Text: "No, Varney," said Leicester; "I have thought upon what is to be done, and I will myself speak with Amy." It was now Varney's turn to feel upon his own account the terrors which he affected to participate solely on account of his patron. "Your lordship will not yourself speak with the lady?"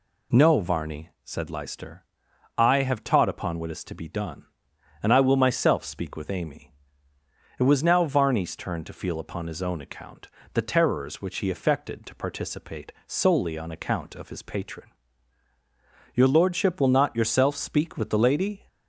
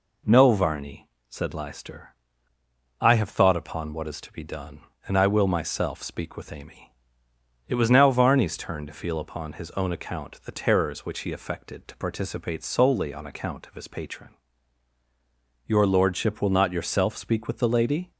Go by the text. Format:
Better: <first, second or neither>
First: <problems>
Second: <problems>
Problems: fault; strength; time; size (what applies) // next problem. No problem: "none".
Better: second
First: says "taught" for "thought"; at 3.0 s // pauses between "account" and "the"; slight; at 10.2 s; 0.26 s long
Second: none